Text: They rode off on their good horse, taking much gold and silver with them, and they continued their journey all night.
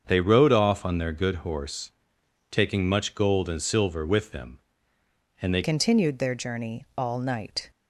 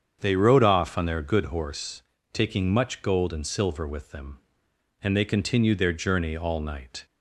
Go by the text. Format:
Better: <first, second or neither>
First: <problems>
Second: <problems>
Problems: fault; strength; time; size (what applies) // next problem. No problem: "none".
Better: second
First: starts louder than the rest; until 1.0 s; 7 dB // changes voice at "continued"; from 5.6 s on; 2.0 s long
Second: starts louder than the rest; strong; until 1.2 s; 7.5 dB